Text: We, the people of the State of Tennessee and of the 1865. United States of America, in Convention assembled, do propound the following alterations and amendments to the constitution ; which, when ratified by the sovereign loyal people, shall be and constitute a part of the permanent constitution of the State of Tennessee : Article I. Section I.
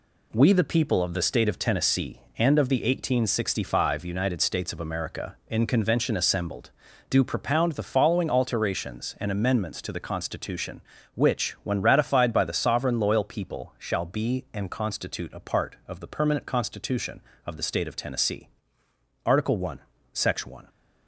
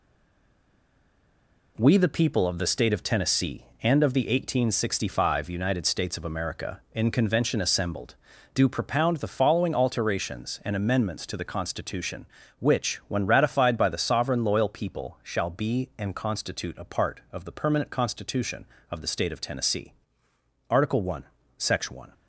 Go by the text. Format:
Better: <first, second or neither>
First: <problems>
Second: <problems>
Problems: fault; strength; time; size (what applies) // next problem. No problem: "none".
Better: first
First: none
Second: stays silent before the first word; noticeable; until 1.7 s; 1.7 s long